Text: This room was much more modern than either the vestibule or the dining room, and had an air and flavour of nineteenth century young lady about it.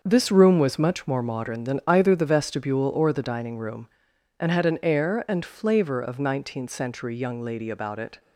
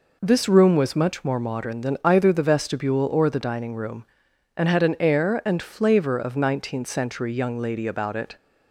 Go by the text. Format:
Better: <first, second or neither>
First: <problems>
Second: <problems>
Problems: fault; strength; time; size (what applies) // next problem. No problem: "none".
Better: second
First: gets quieter; strong; throughout; 9 dB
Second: none